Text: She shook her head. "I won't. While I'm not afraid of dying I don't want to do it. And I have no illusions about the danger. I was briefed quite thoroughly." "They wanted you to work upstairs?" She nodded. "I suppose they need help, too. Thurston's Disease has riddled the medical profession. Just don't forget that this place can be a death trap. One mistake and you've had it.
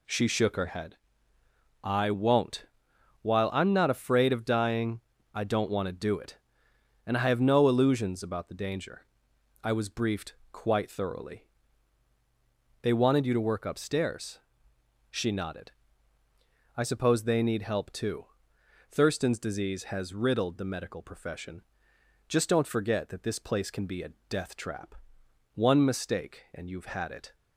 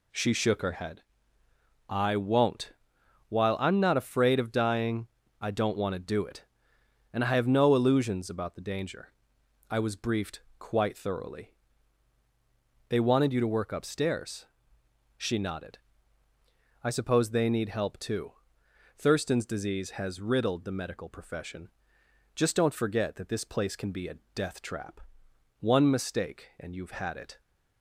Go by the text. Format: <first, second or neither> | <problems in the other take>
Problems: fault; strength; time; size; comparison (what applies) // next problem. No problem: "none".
neither | pauses between "dying" and "I"; slight; the same in both // pauses between "briefed" and "quite"; slight; the same in both // pauses between "a" and "death"; slight; the same in both